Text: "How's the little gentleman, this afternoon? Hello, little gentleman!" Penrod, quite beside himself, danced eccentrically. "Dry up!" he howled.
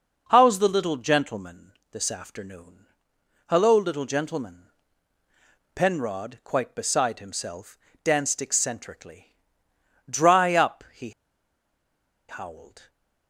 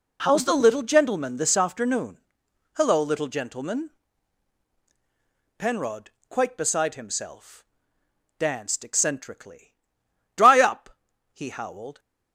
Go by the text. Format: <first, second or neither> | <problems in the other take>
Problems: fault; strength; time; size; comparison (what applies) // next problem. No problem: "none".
second | pauses between "he" and "howled"; at 11.1 s; 1.1 s long